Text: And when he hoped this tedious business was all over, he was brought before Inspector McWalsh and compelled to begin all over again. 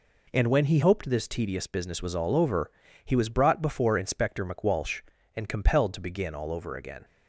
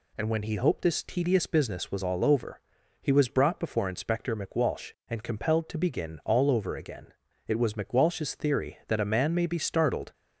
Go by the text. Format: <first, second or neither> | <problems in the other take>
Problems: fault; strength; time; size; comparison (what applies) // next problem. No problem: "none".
first | goes on to say "It was McWalsh's theory that a man may be startled"; strong; from 7.4 s on; 2.6 s long